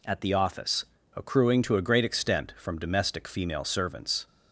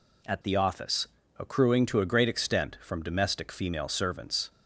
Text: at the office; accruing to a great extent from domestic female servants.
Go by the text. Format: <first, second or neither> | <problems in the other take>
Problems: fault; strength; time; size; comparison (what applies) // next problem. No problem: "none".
neither | none